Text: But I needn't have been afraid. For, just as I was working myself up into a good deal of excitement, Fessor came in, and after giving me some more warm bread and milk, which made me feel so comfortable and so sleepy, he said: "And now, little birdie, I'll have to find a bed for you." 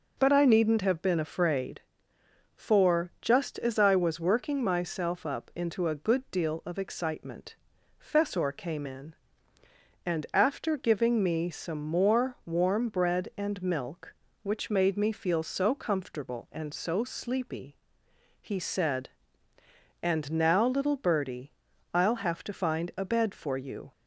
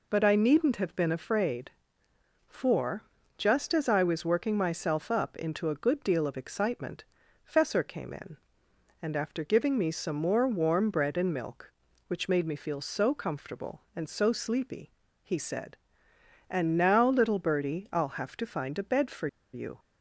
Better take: first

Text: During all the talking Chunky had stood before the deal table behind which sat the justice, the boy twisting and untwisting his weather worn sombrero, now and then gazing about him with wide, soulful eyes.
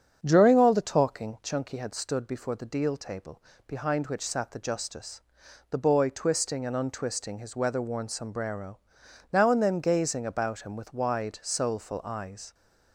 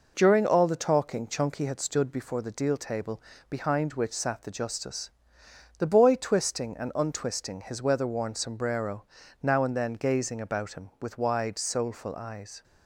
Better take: second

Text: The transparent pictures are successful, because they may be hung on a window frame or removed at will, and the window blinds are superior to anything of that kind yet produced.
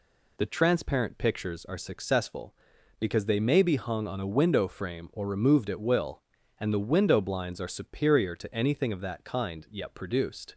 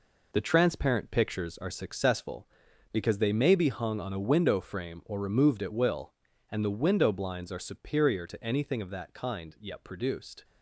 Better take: first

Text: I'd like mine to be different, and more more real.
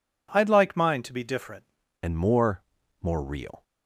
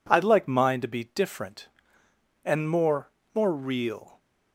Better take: second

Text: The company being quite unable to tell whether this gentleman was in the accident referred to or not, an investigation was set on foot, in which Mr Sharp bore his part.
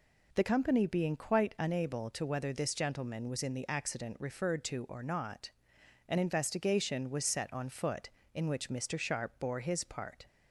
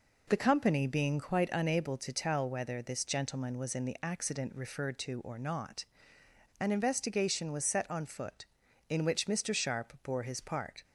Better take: second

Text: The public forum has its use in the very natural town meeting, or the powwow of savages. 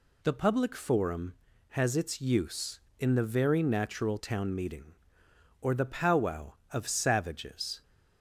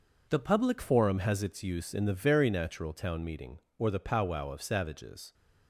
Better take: first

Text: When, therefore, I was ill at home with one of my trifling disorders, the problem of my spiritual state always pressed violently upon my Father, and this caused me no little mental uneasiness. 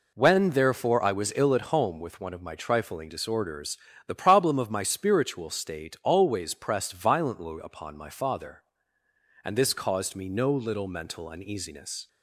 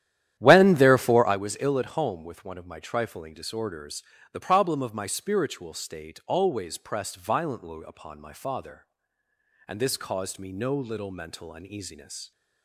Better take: first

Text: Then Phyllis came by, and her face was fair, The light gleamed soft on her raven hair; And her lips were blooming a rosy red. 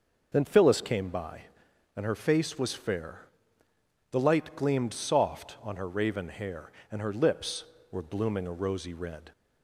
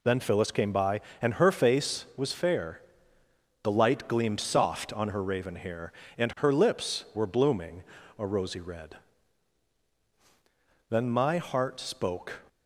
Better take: first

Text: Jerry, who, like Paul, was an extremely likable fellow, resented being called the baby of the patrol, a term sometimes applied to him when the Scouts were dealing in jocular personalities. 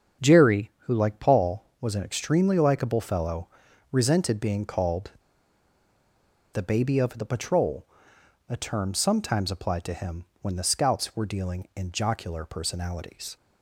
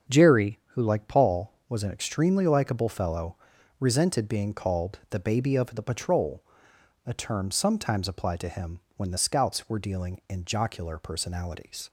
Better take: second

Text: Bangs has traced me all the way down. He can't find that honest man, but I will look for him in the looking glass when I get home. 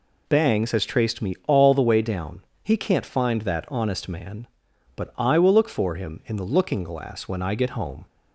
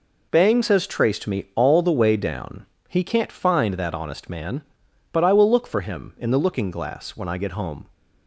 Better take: neither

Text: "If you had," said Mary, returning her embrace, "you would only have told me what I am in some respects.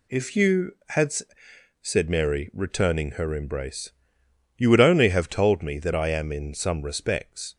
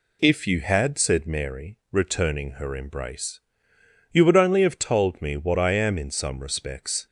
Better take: second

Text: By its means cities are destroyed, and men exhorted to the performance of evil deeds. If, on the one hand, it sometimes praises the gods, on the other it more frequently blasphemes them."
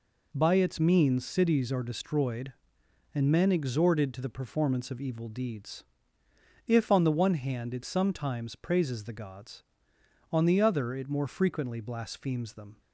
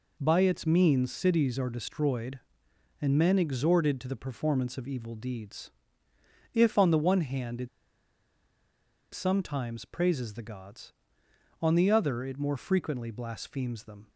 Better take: first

